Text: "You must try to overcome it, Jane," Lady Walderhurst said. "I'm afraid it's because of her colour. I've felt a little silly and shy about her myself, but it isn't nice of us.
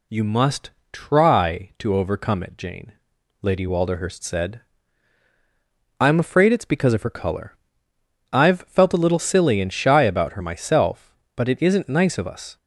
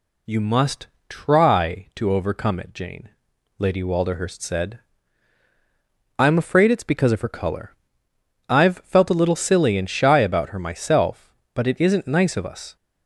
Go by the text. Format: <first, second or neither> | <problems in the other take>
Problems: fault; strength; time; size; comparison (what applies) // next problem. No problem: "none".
neither | pauses between "must" and "try"; slight; the same in both